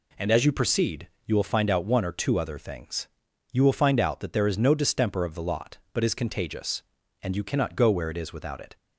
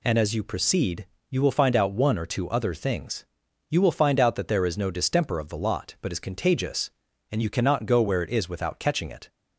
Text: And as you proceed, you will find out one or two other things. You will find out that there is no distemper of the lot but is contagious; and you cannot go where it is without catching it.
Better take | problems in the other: second | skips "catching"; at 8.5 s

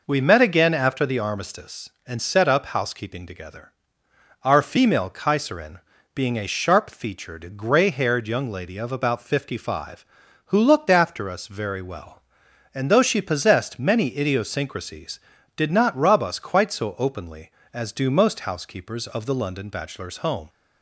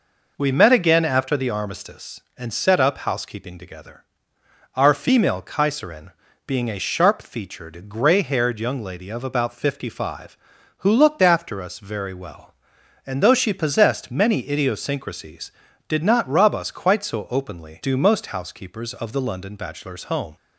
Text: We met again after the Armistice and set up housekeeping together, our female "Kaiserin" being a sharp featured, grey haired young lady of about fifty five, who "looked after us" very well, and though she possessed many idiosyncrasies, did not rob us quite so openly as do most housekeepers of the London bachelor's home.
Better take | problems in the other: first | pauses between "Kaiserin" and "being"; slight; at 6.1 s; 0.34 s long; slight in the first // skips "as"; at 17.8 s

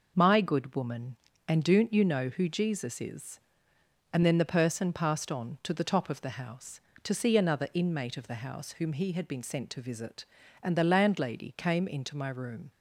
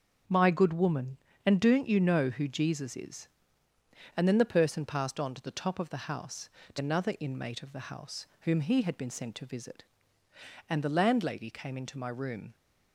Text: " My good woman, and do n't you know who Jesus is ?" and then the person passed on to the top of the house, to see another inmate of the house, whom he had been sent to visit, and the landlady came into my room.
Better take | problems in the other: first | skips "see"; at 6.7 s

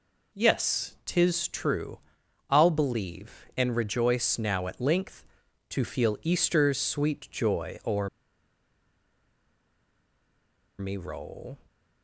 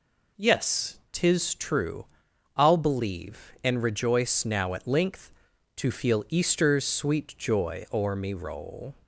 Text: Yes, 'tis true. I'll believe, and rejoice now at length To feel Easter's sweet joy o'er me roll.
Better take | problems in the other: second | pauses between "o'er" and "me"; strong; at 8.0 s; 2.7 s long

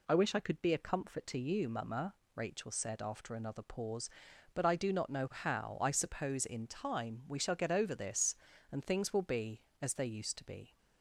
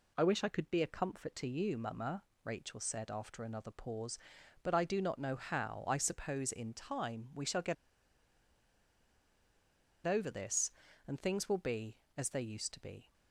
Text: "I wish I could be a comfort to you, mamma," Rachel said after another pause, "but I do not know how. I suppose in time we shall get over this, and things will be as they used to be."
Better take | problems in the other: first | pauses between "get" and "over"; strong; at 7.7 s; 2.3 s long

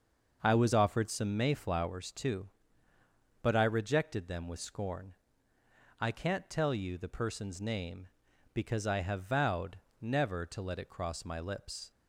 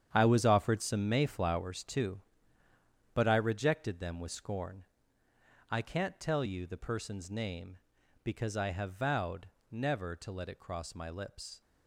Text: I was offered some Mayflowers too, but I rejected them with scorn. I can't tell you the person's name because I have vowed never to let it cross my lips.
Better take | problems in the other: first | gets quieter; strong; throughout; 11 dB // starts louder than the rest; strong; until 1.1 s; 9 dB; also in the first // pauses between "vowed" and "never"; slight; at 9.4 s; 0.22 s long; slight in the first

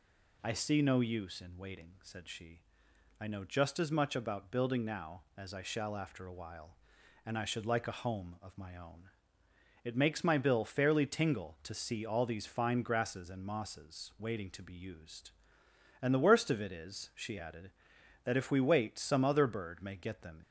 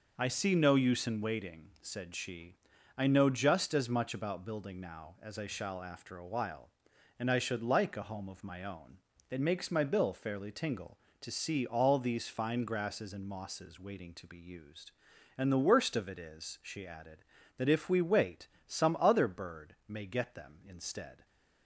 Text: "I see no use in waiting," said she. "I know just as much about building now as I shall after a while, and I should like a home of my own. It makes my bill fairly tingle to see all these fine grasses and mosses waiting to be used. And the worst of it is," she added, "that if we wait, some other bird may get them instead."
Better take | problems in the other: second | stops before "instead"; at 20.4 s

